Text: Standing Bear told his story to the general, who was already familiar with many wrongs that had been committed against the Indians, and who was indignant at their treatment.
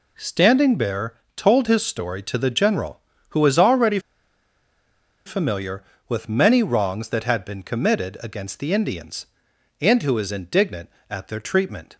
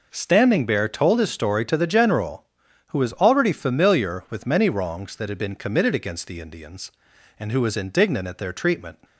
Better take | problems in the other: second | pauses between "Bear" and "told"; slight; at 1.1 s; 0.22 s long // pauses between "already" and "familiar"; strong; at 3.9 s; 1.2 s long

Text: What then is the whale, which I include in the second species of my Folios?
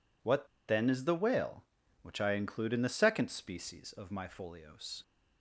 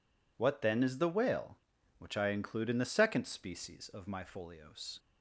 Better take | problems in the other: second | pauses between "What" and "then"; slight; at 0.4 s; 0.21 s long

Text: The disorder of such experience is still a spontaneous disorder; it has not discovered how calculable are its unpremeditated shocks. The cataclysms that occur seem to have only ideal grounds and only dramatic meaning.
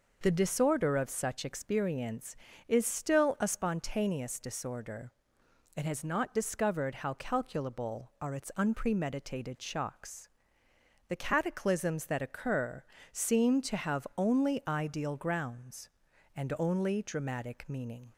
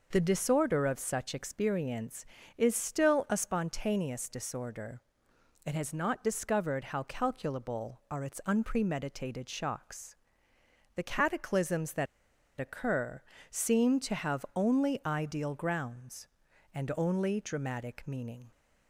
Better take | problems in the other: first | pauses between "that" and "occur"; noticeable; at 12.0 s; 0.54 s long // pauses between "occur" and "seem"; slight; at 13.2 s; 0.28 s long; slight in the first

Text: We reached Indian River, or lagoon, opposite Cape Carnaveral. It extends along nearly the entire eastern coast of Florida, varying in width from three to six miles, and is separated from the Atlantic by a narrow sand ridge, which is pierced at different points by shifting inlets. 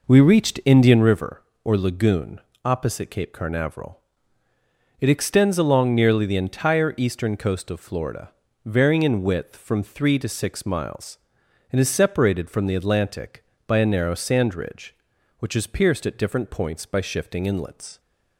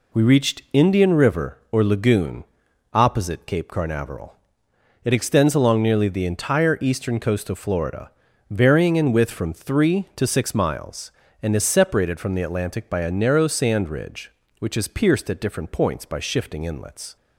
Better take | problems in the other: second | starts louder than the rest; noticeable; until 1.1 s; 5 dB

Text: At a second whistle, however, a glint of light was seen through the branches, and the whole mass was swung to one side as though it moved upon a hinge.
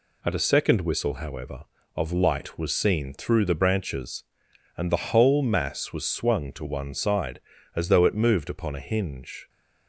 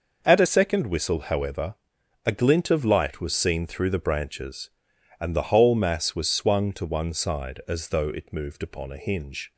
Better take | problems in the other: second | skips "a glint"; at 1.7 s

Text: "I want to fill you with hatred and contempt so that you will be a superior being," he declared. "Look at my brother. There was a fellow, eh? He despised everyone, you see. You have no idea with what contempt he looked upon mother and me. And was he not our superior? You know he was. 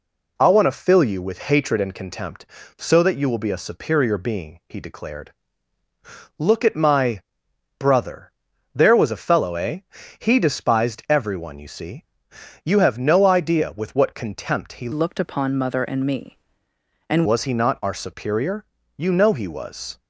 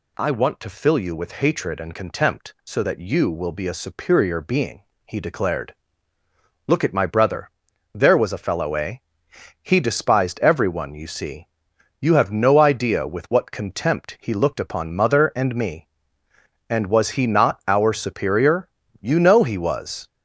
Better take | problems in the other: second | pauses between "my" and "brother"; noticeable; at 7.2 s; 0.56 s long // changes voice from "looked" to "And"; from 14.9 to 17.2 s; 2.3 s long

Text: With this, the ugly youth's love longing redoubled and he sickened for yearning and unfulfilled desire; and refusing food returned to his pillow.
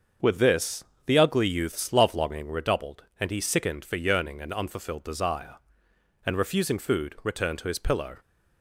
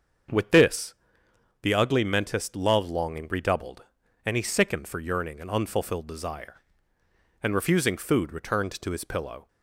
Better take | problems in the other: first | starts louder than the rest; strong; until 2.0 s; 7 dB; also in the first // says "mentist" for "youth's"; at 2.0 s

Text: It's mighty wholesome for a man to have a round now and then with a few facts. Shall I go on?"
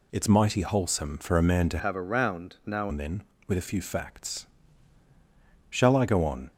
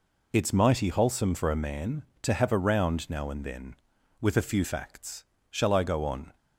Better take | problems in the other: second | changes voice from "have" to "now"; from 1.7 to 2.8 s; 1.1 s long

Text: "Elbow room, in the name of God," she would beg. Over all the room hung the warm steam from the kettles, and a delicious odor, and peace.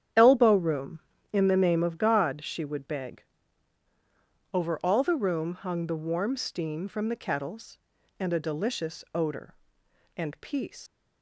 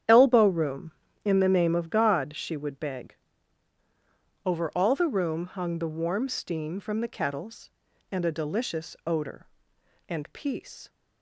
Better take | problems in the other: second | starts louder than the rest; strong; until 1.4 s; 9.5 dB; strong in the second // leaves "peace" unfinished; at 10.8 s; 105 ms

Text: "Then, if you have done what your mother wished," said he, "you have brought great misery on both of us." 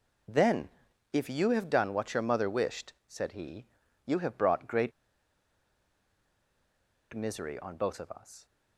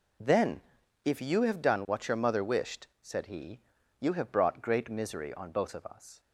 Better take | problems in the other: second | pauses between "great" and "misery"; strong; at 4.9 s; 2.2 s long

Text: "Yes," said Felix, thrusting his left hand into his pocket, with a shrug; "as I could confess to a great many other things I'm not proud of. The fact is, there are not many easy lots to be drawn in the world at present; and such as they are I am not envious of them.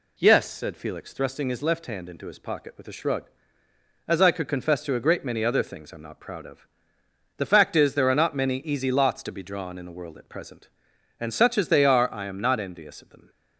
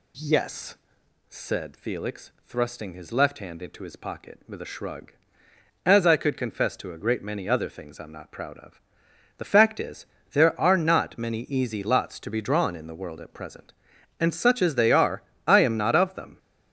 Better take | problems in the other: first | pauses between "are" and "I"; slight; at 15.2 s; 0.24 s long // skips "envious"; at 15.9 s

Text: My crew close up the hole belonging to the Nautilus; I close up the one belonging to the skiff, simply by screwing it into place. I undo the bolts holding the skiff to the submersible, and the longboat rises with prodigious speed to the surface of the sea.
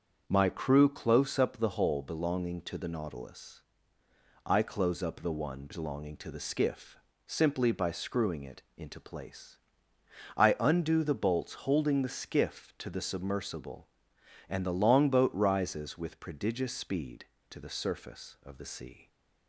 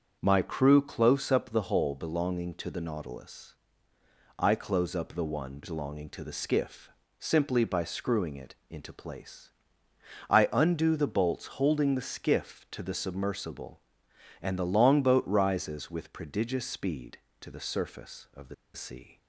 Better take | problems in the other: first | starts louder than the rest; until 1.2 s; 7 dB; also in the first // pauses between "the" and "sea"; slight; at 18.5 s; 0.20 s long

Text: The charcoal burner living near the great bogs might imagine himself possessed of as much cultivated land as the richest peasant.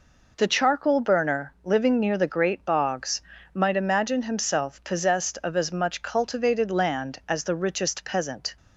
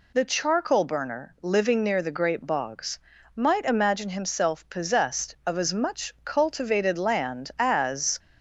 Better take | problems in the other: first | pauses between "bogs" and "might"; at 2.9 s; 0.38 s long; slight in the first // stops before "the richest peasant"; at 8.1 s

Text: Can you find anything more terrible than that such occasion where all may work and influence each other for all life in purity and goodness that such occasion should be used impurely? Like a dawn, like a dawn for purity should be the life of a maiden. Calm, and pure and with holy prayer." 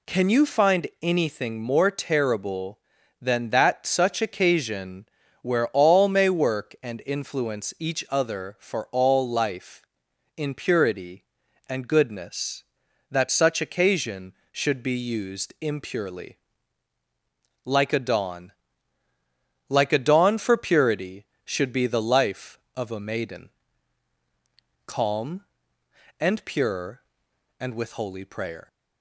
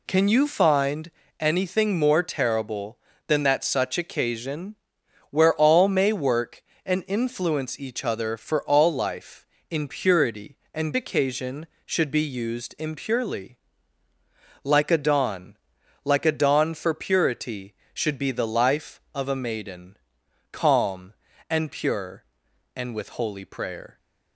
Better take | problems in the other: first | pauses between "find" and "anything"; slight; at 1.1 s; 0.30 s long // pauses between "occasion" and "where"; noticeable; at 4.7 s; 0.54 s long; slight in the first // skips "goodness that such"; at 10.9 s

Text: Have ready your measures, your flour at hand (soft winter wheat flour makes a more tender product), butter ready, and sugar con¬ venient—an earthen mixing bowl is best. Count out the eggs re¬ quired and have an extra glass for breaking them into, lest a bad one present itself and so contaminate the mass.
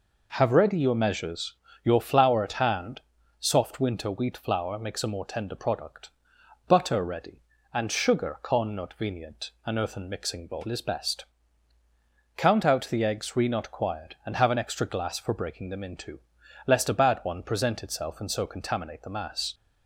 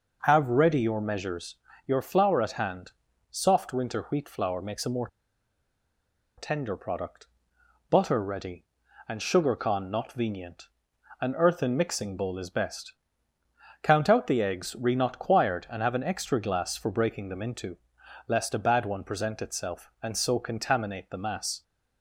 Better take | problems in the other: first | pauses between "more" and "tender"; strong; at 5.0 s; 1.3 s long

